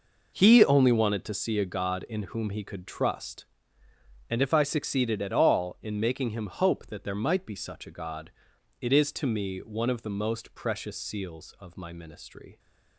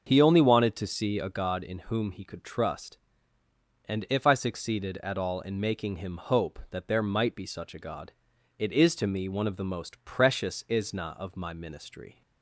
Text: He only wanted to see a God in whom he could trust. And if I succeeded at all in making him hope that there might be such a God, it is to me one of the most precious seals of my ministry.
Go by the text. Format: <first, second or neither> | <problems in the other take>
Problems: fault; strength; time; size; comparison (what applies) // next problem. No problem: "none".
first | starts louder than the rest; until 1.1 s; 6.5 dB // says "isna" for "seals"; at 10.6 s